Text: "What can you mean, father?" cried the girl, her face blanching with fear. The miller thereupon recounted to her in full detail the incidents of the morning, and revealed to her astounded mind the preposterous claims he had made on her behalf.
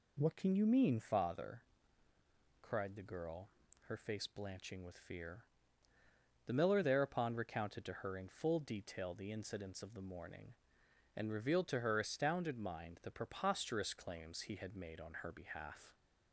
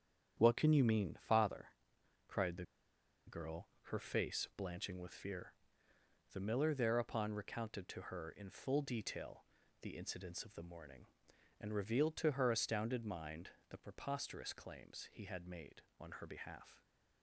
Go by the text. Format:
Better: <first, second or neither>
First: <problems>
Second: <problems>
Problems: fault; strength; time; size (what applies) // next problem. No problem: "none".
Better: first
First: none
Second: starts louder than the rest; strong; until 1.3 s; 8.5 dB // pauses between "the" and "girl"; noticeable; at 2.6 s; 0.62 s long // pauses between "detail" and "the"; slight; at 9.4 s; 0.34 s long // pauses between "mind" and "the"; slight; at 13.5 s; 0.18 s long